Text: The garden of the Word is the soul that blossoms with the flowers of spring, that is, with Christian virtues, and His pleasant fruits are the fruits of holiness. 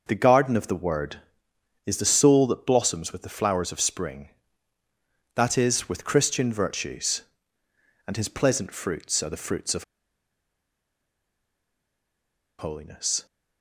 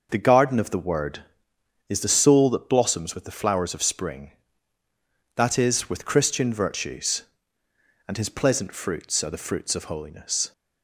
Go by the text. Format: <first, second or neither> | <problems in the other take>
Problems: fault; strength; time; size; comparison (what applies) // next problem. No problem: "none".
second | pauses between "of" and "holiness"; strong; at 9.8 s; 2.7 s long